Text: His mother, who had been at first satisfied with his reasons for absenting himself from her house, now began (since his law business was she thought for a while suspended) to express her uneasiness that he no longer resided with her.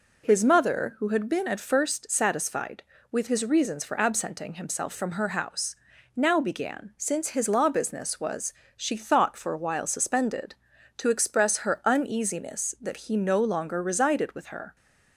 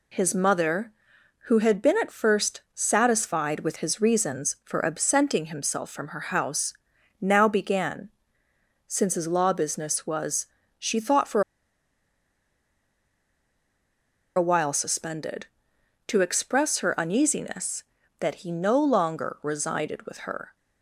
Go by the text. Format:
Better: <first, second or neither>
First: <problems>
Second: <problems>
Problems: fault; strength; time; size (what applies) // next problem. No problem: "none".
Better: first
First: pauses between "was" and "she"; slight; at 8.5 s; 0.24 s long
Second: pauses between "was" and "she"; slight; at 10.4 s; 0.34 s long // pauses between "for" and "a"; strong; at 11.4 s; 2.9 s long